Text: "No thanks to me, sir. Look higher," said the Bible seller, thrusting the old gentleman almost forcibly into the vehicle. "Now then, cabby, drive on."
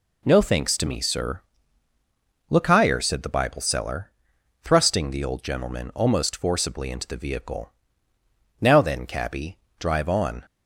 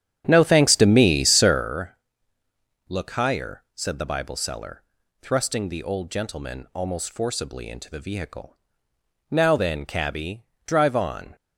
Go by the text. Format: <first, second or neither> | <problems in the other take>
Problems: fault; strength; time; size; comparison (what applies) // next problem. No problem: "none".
first | starts louder than the rest; strong; until 1.7 s; 10 dB